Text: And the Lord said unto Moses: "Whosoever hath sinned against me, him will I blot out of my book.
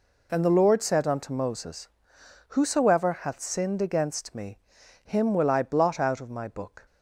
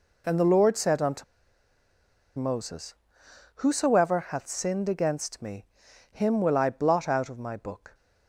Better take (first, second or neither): first